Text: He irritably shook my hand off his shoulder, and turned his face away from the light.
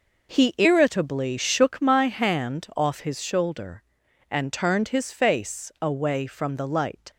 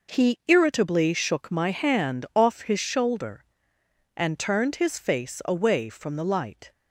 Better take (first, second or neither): neither